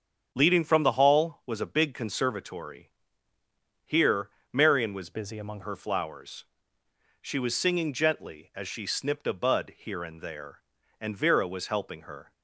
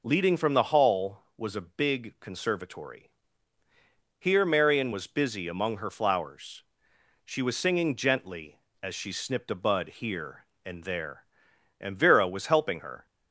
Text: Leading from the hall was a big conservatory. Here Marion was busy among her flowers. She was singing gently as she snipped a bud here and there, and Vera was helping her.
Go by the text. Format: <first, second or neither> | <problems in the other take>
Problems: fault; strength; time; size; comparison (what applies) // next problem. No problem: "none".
second | starts louder than the rest; until 1.3 s; 7 dB // pauses between "Here" and "Marion"; slight; at 4.3 s; 0.20 s long // changes voice from "busy" to "among"; from 5.1 to 5.6 s; 0.5 s long